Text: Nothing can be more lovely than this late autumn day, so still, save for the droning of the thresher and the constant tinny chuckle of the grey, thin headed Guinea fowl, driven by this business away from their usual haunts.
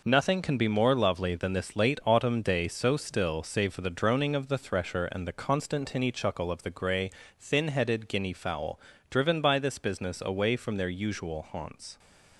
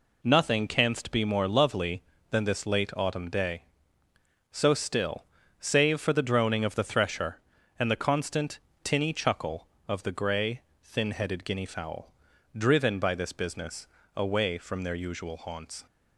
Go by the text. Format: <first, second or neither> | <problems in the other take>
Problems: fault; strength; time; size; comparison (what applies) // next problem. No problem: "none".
first | says "canst" for "can"; at 0.6 s // pauses between "constant" and "tinny"; slight; at 8.5 s; 0.24 s long // pauses between "business" and "away"; slight; at 13.8 s; 0.26 s long